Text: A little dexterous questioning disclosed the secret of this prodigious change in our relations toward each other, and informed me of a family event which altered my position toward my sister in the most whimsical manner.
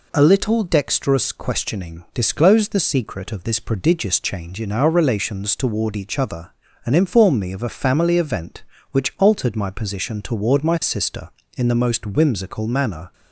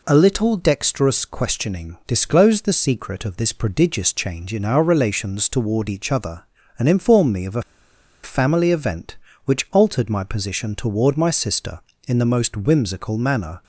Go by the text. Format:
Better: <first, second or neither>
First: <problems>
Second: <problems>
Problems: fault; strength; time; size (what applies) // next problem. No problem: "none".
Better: first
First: none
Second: pauses between "a" and "family"; noticeable; at 7.6 s; 0.61 s long